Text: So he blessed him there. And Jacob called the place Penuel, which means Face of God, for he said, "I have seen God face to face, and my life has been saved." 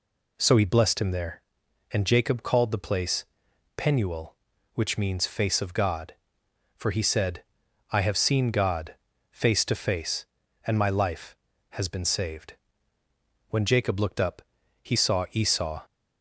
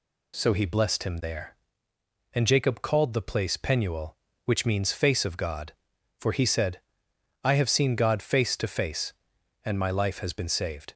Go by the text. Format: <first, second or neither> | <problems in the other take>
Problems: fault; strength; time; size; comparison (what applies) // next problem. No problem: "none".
second | pauses between "place" and "Penuel"; noticeable; at 3.2 s; 0.52 s long // pauses between "God" and "face"; slight; at 8.9 s; 0.34 s long // goes on to say "When Jacob looked up he saw Esau"; strong; from 13.4 s on; 2.3 s long